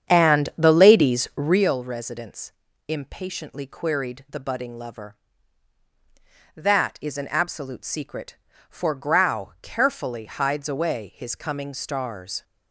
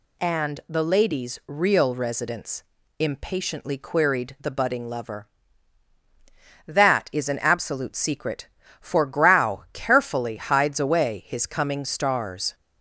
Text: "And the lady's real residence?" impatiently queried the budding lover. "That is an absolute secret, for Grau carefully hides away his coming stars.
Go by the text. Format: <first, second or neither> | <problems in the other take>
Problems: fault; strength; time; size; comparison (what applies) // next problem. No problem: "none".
second | starts louder than the rest; strong; until 1.7 s; 8 dB